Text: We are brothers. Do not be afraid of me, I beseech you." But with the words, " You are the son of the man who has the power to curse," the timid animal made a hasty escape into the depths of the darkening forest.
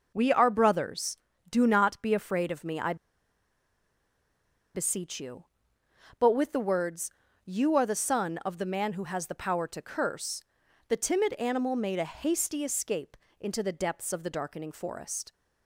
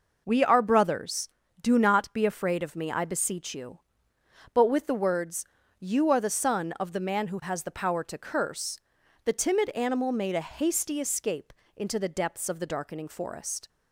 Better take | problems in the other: second | pauses between "I" and "beseech"; strong; at 2.9 s; 1.8 s long // pauses between "escape" and "into"; slight; at 13.1 s; 0.24 s long; slight in the second

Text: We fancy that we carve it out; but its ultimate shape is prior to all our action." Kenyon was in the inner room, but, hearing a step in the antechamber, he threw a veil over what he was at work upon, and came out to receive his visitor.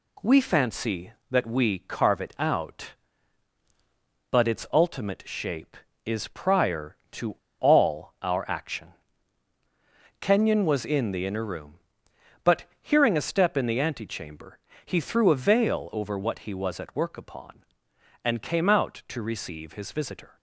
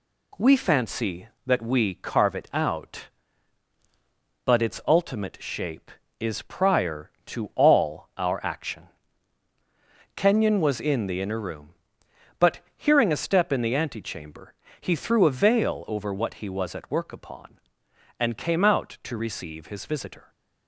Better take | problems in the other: second | pauses between "to" and "all"; slight; at 7.3 s; 0.23 s long

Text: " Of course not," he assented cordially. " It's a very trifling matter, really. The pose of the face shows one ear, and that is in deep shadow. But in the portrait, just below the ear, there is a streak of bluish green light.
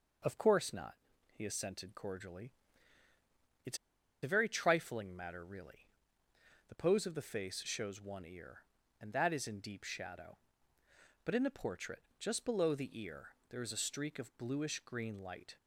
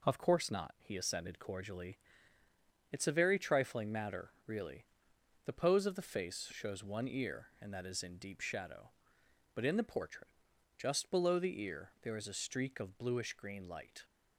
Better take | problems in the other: second | pauses between "It's" and "a"; at 3.7 s; 0.45 s long

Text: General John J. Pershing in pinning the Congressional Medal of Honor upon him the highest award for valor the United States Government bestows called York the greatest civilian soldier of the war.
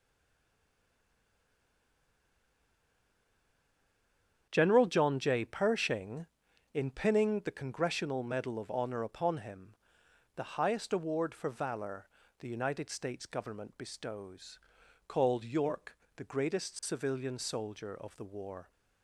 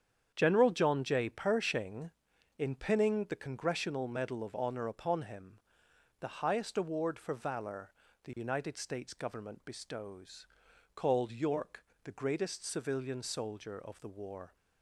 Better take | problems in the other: second | stays silent before the first word; strong; until 4.4 s; 4.4 s long // starts louder than the rest; strong; until 5.5 s; 8 dB; strong in the second // pauses between "him" and "the"; noticeable; at 9.7 s; 0.62 s long; noticeable in the second // pauses between "valor" and "the"; slight; at 12.0 s; 0.34 s long; slight in the second // pauses between "bestows" and "called"; noticeable; at 14.5 s; 0.48 s long; noticeable in the second // pauses between "York" and "the"; slight; at 15.9 s; 0.18 s long; slight in the second

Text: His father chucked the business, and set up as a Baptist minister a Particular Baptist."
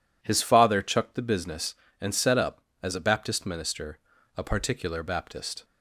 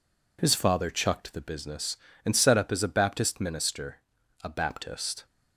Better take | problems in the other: first | pauses between "minister" and "a"; at 3.9 s; 0.44 s long; also in the first // skips "Particular"; at 4.4 s

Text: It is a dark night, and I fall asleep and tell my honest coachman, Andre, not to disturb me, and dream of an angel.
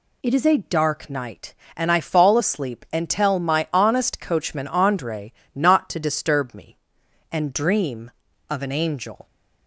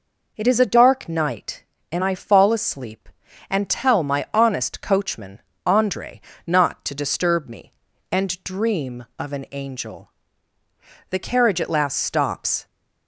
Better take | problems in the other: first | goes on to say "The carriage at last stops"; from 11.0 s on; 1.5 s long

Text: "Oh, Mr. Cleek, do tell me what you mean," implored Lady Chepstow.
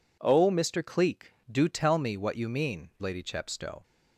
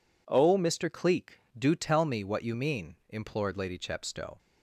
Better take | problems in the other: second | skips "implored"; at 2.9 s

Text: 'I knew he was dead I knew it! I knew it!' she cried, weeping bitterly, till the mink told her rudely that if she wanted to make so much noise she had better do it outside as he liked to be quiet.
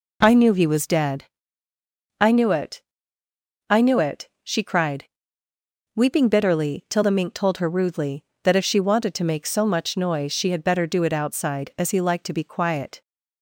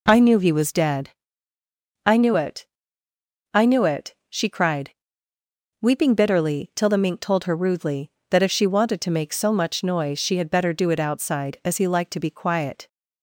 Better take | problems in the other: neither | pauses between "dead" and "I"; noticeable; the same in both

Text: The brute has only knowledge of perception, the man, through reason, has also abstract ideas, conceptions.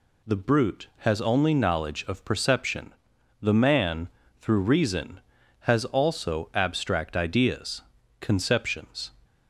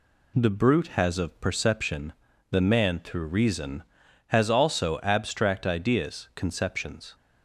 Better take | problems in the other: first | skips "only knowledge"; at 1.1 s

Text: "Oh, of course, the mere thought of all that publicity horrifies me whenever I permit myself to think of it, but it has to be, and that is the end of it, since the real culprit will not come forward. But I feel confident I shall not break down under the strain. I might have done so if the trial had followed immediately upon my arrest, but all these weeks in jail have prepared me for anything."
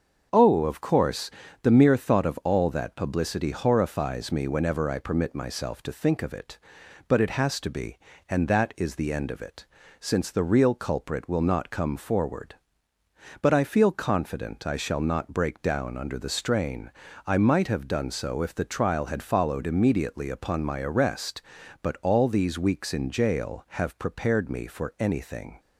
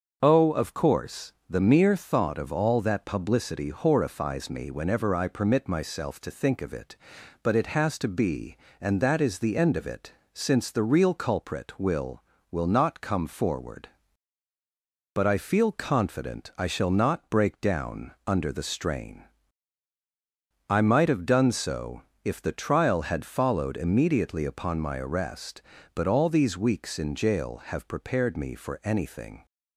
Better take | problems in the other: first | starts louder than the rest; until 1.2 s; 6.5 dB; also in the first // says "will" twice; at 12.5 s // pauses between "down" and "under"; slight; at 18.1 s; 0.16 s long // pauses between "so" and "if"; slight; at 22.0 s; 0.24 s long

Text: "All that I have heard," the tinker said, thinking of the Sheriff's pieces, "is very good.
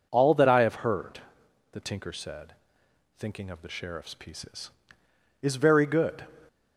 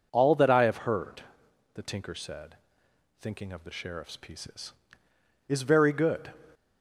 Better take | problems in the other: neither | none

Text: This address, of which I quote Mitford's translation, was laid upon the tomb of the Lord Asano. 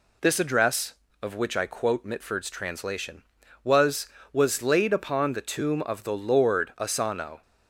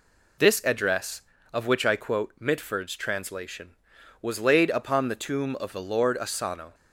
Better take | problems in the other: second | says "was" twice; at 4.3 s

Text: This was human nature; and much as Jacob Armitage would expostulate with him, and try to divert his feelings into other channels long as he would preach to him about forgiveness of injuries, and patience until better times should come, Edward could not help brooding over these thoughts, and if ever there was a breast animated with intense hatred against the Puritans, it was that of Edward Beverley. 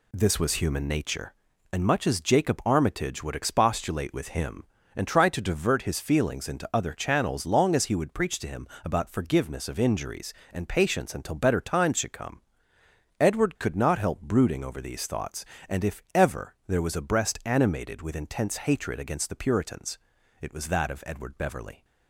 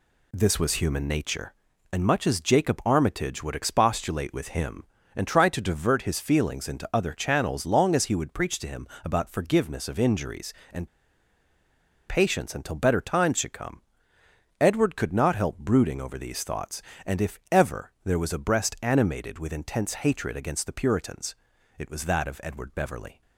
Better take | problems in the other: first | pauses between "him" and "about"; slight; at 8.8 s; 0.16 s long; slight in the first // pauses between "and" and "patience"; at 10.8 s; 1.2 s long

